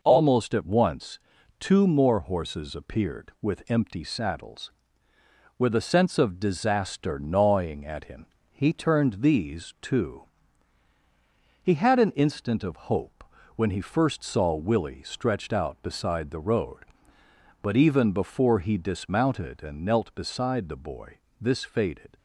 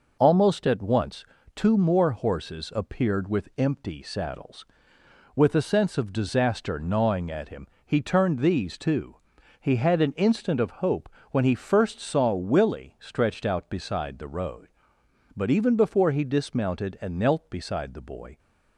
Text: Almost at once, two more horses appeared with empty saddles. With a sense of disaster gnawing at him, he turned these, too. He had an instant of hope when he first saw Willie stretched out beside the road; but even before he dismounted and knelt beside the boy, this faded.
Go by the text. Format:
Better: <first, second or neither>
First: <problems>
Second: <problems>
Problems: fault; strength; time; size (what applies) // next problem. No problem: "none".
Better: first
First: pauses between "hope" and "when"; slight; at 13.2 s; 0.32 s long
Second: pauses between "hope" and "when"; slight; at 11.0 s; 0.22 s long // stops before "this faded"; at 18.3 s